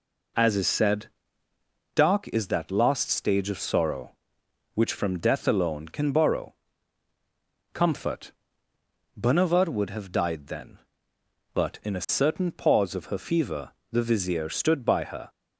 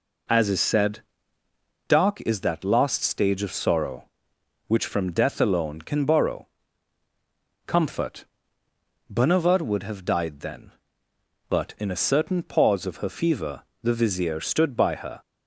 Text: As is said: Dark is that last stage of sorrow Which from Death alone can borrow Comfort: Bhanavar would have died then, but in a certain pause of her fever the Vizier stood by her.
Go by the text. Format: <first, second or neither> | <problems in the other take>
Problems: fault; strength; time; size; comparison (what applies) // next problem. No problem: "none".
neither | pauses between "borrow" and "Comfort"; the same in both // pauses between "fever" and "the"; slight; the same in both